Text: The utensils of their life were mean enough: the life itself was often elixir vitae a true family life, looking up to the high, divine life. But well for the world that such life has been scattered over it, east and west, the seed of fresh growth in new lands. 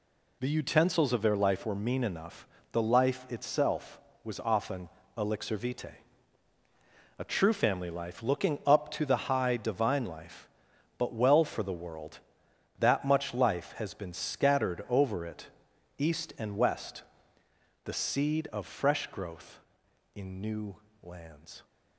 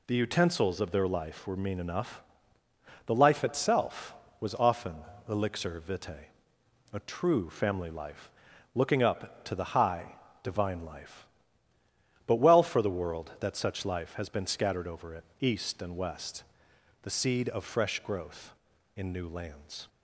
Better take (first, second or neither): second